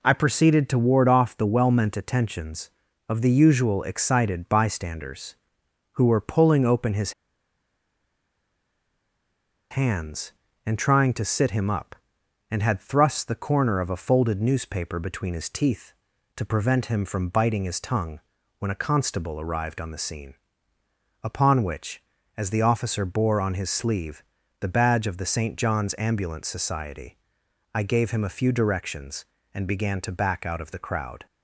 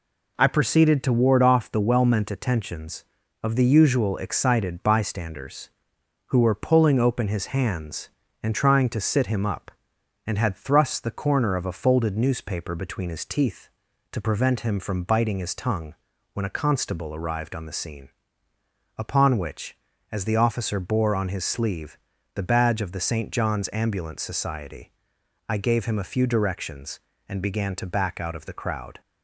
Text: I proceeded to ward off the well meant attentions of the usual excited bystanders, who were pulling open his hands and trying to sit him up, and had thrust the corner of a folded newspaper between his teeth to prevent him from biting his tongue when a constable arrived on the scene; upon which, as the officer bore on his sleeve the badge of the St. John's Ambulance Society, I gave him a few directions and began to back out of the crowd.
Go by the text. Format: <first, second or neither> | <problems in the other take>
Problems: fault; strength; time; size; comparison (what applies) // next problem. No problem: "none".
second | pauses between "his" and "hands"; strong; at 7.1 s; 2.5 s long // pauses between "tongue" and "when"; at 18.1 s; 0.38 s long; also in the second // pauses between "sleeve" and "the"; at 24.2 s; 0.38 s long; also in the second